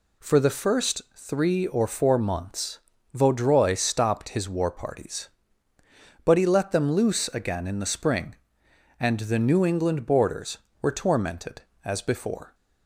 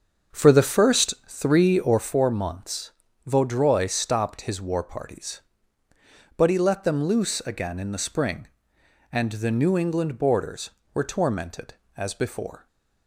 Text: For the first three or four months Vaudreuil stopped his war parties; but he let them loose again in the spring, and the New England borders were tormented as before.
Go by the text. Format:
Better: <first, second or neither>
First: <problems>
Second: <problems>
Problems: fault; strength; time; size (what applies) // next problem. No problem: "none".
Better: first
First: pauses between "months" and "Vaudreuil"; slight; at 2.7 s; 0.36 s long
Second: starts louder than the rest; until 2.1 s; 6.5 dB // pauses between "months" and "Vaudreuil"; slight; at 2.9 s; 0.36 s long